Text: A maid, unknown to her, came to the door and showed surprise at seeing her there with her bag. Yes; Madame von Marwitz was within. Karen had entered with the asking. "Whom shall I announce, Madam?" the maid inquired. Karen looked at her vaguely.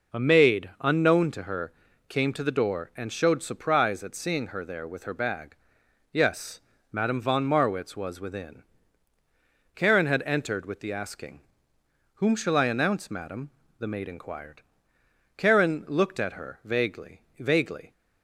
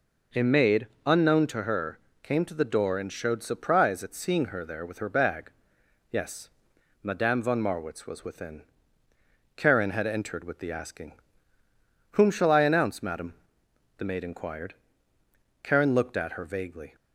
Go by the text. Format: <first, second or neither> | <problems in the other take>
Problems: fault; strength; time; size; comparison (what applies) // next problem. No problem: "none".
second | says "vaguely" twice; at 17.3 s